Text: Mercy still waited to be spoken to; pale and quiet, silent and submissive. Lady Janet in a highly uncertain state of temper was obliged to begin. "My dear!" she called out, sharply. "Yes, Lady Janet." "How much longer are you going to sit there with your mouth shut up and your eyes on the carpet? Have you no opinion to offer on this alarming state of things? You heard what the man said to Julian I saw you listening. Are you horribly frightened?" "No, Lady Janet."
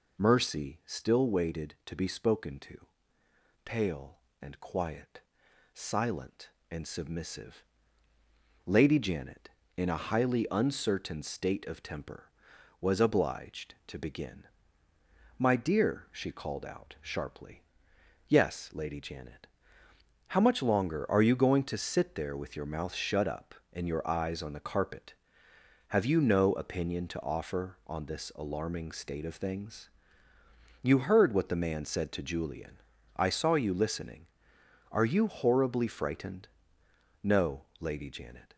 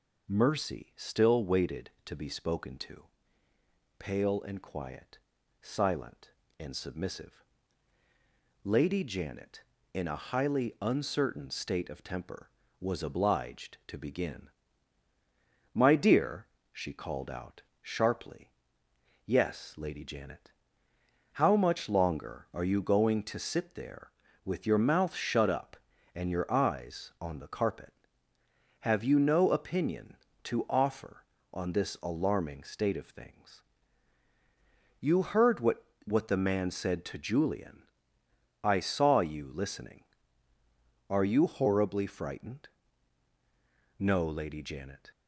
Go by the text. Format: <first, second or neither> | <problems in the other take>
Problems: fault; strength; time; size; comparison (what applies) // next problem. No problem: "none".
first | says "what" twice; at 36.0 s // pauses between "Julian" and "I"; noticeable; at 37.8 s; 0.80 s long; also in the first